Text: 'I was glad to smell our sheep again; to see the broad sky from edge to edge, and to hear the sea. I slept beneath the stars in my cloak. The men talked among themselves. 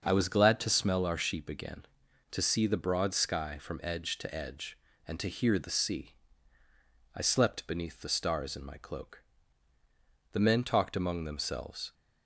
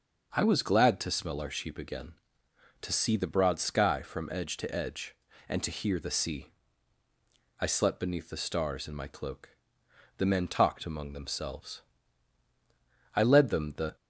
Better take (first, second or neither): first